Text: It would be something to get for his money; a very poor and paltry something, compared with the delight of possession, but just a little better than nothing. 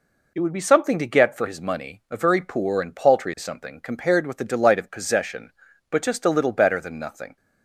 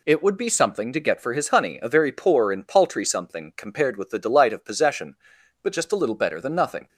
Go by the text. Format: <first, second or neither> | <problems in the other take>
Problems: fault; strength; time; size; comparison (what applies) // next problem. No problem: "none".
first | says "honey" for "money"; at 1.4 s